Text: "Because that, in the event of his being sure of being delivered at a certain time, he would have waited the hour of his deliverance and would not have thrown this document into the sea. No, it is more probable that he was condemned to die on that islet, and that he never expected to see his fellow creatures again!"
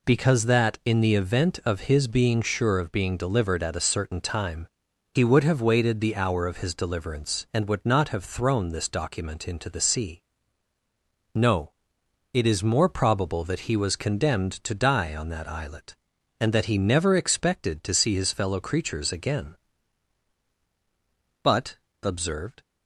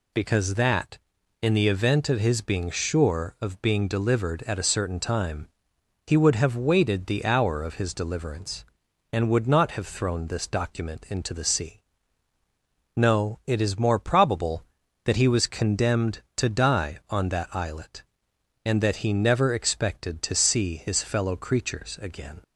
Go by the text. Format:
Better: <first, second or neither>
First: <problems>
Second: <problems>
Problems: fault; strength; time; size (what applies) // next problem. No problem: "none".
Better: second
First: goes on to say "But observed"; noticeable; from 21.4 s on; 1.2 s long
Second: none